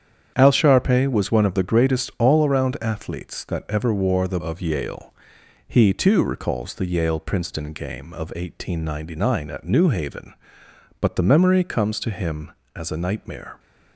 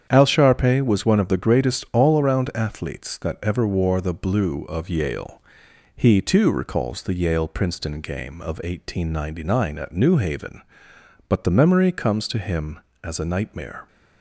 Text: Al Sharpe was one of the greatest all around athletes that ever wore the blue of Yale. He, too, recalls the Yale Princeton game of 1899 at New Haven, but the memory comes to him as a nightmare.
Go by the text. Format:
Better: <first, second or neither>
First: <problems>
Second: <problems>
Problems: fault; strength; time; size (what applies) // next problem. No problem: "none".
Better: second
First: starts louder than the rest; strong; until 1.3 s; 8.5 dB // skips "blue"; at 4.3 s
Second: starts louder than the rest; strong; until 1.1 s; 8.5 dB